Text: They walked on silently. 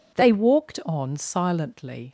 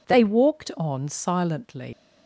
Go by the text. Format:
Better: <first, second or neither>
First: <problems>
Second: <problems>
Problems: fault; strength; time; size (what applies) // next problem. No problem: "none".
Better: first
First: none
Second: leaves "silently" unfinished; at 1.9 s; 95 ms